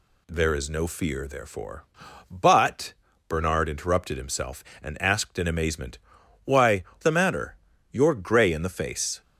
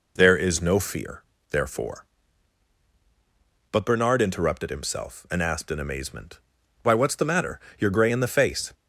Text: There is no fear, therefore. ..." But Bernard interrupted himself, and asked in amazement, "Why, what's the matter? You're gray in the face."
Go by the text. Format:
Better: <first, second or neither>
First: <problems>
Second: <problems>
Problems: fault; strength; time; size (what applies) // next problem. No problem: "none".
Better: second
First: pauses between "But" and "Bernard"; slight; at 2.9 s; 0.34 s long // skips "what's"; at 6.9 s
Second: none